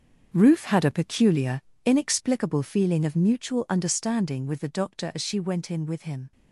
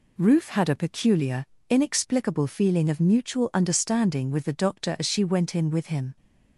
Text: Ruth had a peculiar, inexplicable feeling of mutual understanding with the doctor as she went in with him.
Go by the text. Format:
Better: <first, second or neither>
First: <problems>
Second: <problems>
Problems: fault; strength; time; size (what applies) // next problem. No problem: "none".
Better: second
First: gets quieter; strong; throughout; 11.5 dB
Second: none